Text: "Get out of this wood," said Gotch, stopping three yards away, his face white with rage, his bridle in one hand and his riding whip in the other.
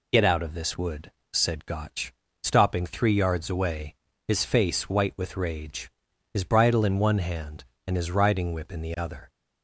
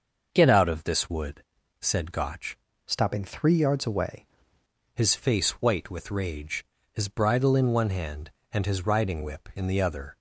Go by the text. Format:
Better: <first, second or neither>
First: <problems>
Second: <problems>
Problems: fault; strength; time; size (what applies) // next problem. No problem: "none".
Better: first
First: none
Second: starts louder than the rest; until 1.3 s; 6 dB // changes voice from "stopping" to "away"; from 2.8 to 4.2 s; 1.4 s long